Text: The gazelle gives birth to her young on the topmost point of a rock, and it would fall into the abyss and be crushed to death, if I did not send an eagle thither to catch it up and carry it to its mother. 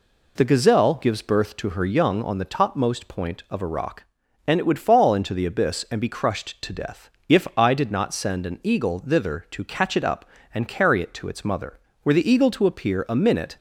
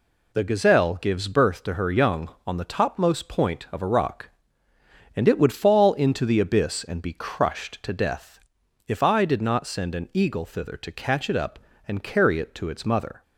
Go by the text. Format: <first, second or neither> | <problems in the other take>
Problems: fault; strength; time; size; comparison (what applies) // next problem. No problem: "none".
second | goes on to say "Were the eagle to appear a minute"; from 12.0 s on; 1.5 s long